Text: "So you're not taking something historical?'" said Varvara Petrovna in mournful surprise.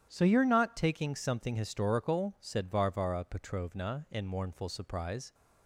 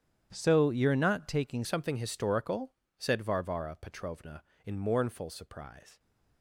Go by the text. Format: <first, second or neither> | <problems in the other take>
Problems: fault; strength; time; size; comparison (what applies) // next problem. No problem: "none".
first | starts louder than the rest; strong; until 1.3 s; 9.5 dB; strong in the first // changes voice at "something"; from 1.6 s on; 4.3 s long